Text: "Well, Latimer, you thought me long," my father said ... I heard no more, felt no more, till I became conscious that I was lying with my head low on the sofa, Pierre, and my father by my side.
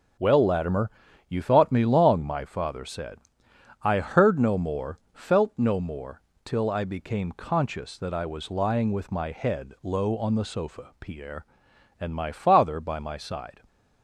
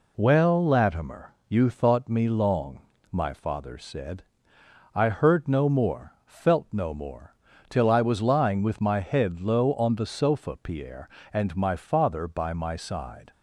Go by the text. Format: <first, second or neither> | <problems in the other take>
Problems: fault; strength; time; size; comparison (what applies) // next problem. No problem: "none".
first | skips "I became conscious that"; at 7.8 s